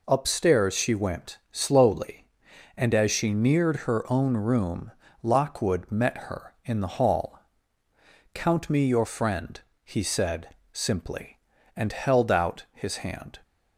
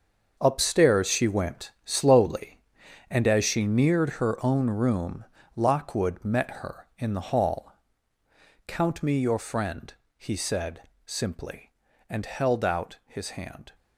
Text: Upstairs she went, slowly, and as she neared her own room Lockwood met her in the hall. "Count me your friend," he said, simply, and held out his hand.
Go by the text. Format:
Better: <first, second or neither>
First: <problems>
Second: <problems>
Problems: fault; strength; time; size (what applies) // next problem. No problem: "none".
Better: first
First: pauses between "room" and "Lockwood"; slight; at 4.9 s; 0.30 s long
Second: gets quieter; strong; throughout; 11.5 dB // pauses between "room" and "Lockwood"; slight; at 5.2 s; 0.30 s long